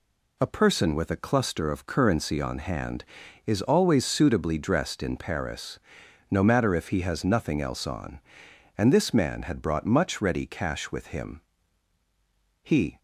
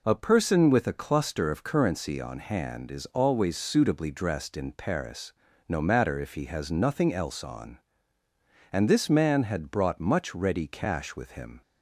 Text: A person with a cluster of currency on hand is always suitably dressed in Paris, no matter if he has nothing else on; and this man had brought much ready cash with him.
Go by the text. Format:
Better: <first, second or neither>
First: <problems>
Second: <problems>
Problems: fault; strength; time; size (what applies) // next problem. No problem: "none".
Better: second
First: goes on to say "He"; slight; from 12.6 s on; 0.34 s long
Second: none